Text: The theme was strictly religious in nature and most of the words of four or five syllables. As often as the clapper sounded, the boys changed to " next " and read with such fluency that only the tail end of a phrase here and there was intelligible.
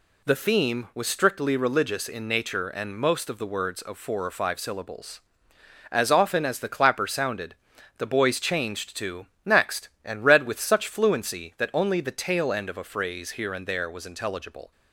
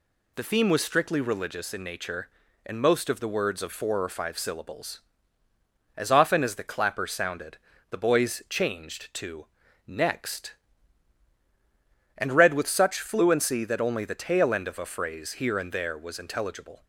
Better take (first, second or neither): neither